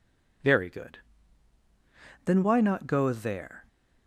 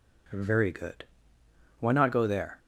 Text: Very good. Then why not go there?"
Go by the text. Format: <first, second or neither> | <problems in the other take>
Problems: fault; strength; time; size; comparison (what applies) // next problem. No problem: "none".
first | skips "Then"; at 1.4 s